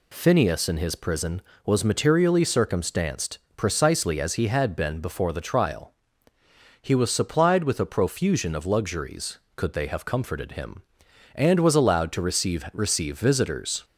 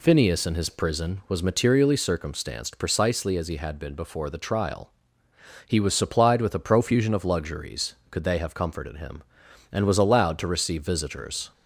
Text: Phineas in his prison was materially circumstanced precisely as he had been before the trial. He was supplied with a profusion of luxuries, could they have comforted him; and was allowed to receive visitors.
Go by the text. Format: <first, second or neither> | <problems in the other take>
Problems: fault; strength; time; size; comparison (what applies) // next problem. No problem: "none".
second | pauses between "circumstanced" and "precisely"; slight; at 3.3 s; 0.18 s long // says "receive" twice; at 12.7 s